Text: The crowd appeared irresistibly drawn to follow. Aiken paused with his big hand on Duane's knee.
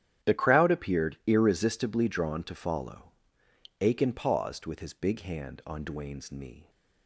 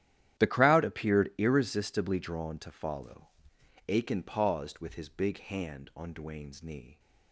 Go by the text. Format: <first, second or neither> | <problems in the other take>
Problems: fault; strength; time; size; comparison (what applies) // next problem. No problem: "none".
neither | starts louder than the rest; strong; the same in both